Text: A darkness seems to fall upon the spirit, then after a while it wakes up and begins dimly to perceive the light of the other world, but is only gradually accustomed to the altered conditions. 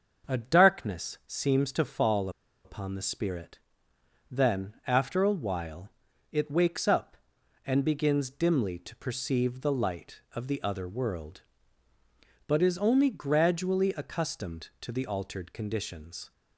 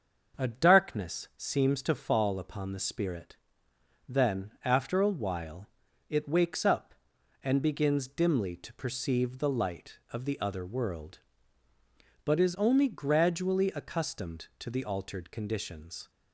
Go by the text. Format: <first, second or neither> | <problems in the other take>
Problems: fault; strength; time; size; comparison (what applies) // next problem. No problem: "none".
second | starts louder than the rest; until 1.3 s; 6.5 dB; also in the second // pauses between "fall" and "upon"; slight; at 2.2 s; 0.35 s long // pauses between "while" and "it"; at 5.8 s; 0.42 s long; also in the second